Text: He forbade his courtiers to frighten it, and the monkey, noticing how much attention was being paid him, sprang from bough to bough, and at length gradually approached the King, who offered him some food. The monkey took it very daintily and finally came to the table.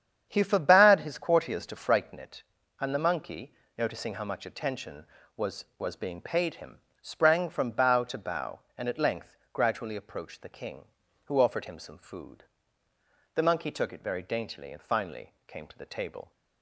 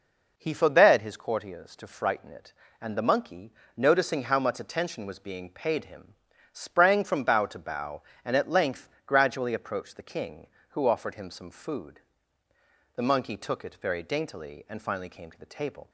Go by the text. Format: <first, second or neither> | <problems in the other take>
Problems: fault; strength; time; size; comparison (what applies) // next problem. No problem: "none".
second | starts louder than the rest; strong; until 1.3 s; 8.5 dB // says "was" twice; at 5.7 s // pauses between "length" and "gradually"; slight; at 9.3 s; 0.18 s long; slight in the second // pauses between "finally" and "came"; slight; at 15.3 s; 0.16 s long